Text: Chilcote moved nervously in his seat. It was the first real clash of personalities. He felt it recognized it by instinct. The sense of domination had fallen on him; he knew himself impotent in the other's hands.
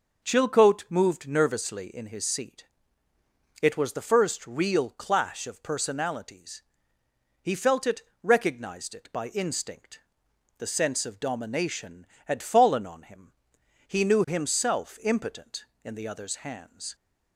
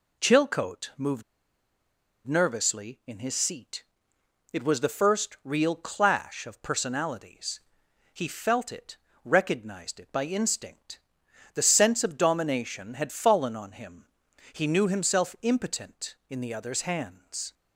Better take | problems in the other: first | pauses between "moved" and "nervously"; at 1.2 s; 1.0 s long // pauses between "it" and "recognized"; slight; at 8.9 s; 0.26 s long; slight in the first

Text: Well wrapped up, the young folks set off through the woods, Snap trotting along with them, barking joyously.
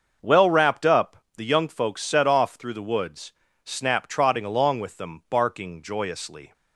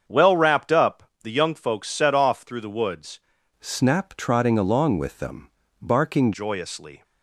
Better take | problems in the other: first | starts louder than the rest; strong; until 1.2 s; 7.5 dB; also in the first // changes voice from "Snap" to "barking"; from 3.5 to 6.3 s; 2.8 s long

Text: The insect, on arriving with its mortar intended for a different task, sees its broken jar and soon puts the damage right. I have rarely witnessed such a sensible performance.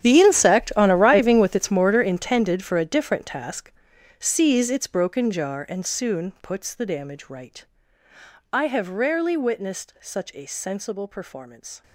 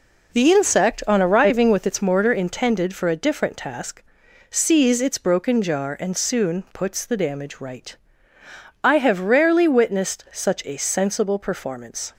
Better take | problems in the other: second | gets quieter; strong; throughout; 17 dB

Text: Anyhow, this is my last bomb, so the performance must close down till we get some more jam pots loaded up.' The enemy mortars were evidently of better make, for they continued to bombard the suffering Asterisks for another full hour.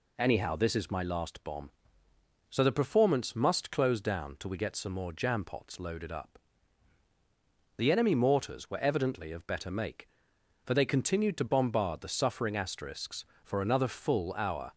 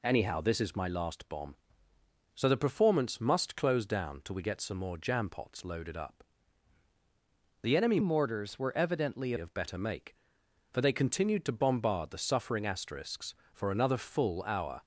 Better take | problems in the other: first | changes voice from "mortars" to "evidently"; from 8.0 to 9.3 s; 1.3 s long

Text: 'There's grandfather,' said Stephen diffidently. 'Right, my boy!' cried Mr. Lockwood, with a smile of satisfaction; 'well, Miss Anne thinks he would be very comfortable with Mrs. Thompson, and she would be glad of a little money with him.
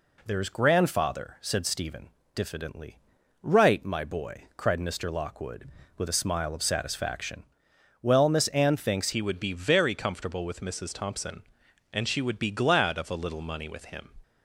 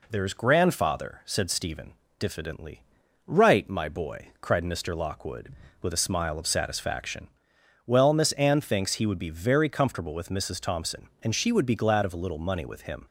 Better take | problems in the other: second | pauses between "Stephen" and "diffidently"; slight; at 2.0 s; 0.26 s long; slight in the second // changes voice at "he"; from 9.1 s on; 4.9 s long

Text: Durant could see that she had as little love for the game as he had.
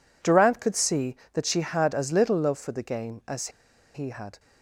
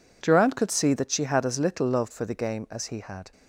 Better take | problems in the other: second | pauses between "as" and "he"; at 3.4 s; 0.45 s long

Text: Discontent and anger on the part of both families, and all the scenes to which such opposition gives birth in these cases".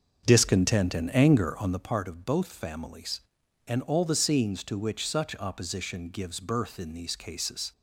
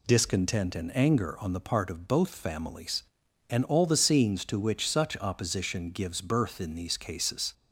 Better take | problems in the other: second | starts louder than the rest; until 1.9 s; 6.5 dB

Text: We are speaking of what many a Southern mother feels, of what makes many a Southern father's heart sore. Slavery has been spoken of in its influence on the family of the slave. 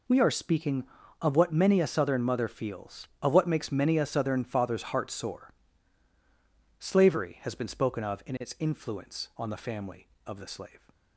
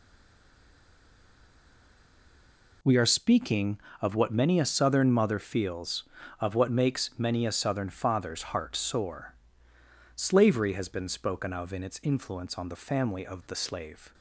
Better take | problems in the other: first | stays silent before the first word; strong; until 2.8 s; 2.8 s long

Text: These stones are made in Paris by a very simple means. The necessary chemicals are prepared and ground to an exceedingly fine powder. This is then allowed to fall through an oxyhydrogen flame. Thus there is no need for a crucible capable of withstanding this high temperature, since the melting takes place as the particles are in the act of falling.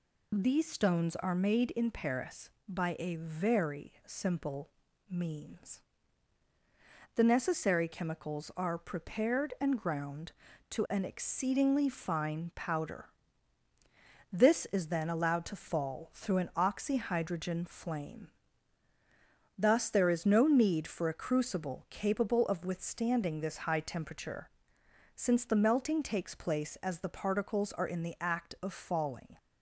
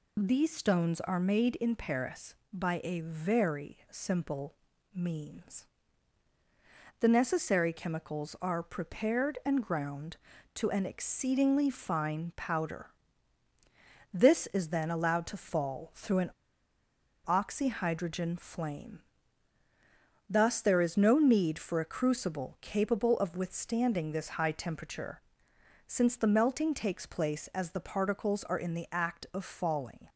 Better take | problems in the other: first | pauses between "simple" and "means"; slight; at 4.5 s; 0.36 s long; slight in the first // pauses between "an" and "oxyhydrogen"; noticeable; at 16.3 s; 0.96 s long

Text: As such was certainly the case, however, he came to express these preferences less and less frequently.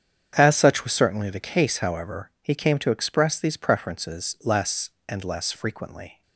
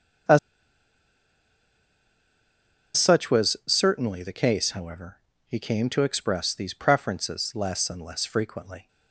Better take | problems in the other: first | starts louder than the rest; strong; until 3.9 s; 7.5 dB; strong in the first // pauses between "As" and "such"; strong; at 0.3 s; 2.5 s long

